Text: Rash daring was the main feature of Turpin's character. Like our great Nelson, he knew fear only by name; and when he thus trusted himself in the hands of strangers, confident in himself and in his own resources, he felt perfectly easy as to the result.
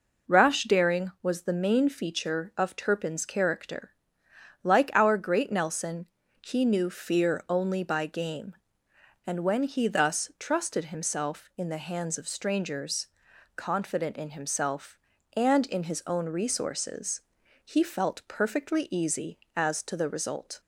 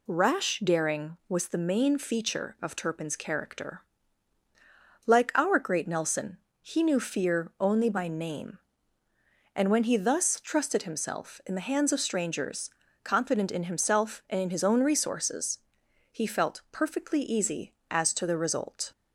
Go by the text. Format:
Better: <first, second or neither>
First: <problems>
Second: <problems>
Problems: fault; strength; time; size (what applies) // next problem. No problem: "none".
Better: second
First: says "game" for "name"; at 8.0 s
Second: none